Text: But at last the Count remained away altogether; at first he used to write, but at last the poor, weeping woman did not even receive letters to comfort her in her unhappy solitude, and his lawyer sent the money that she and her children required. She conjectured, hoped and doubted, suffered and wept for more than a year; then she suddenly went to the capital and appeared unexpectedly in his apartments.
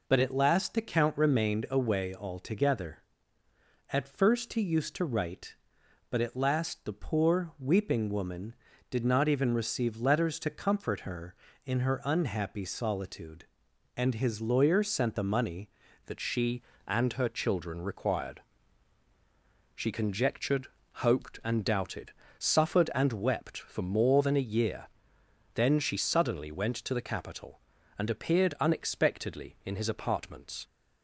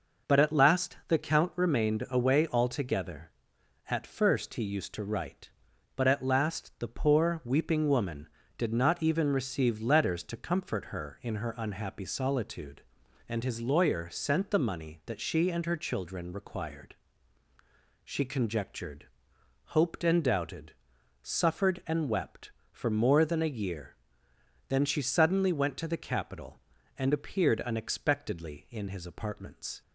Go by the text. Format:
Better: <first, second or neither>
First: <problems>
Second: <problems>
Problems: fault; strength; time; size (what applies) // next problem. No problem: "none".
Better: second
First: changes voice at "that"; from 16.0 s on; 14.6 s long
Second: none